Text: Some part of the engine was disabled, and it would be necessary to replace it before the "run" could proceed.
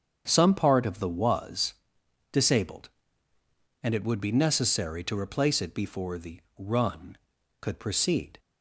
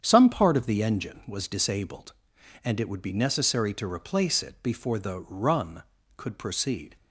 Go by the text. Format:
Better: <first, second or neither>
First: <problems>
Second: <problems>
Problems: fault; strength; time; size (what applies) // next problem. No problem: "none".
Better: second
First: starts louder than the rest; strong; until 1.2 s; 7.5 dB // skips "engine"; at 1.0 s // pauses between "was" and "disabled"; noticeable; at 1.7 s; 0.58 s long // pauses between "the" and "run"; slight; at 6.4 s; 0.17 s long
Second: starts louder than the rest; strong; until 1.0 s; 8.5 dB